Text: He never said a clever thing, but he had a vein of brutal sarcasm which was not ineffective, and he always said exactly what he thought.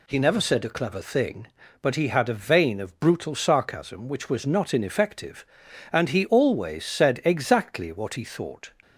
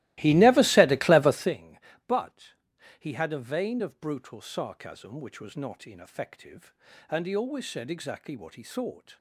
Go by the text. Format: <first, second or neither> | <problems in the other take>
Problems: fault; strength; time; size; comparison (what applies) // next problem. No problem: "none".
first | starts louder than the rest; strong; until 1.5 s; 17.5 dB // pauses between "but" and "he"; at 2.5 s; 0.44 s long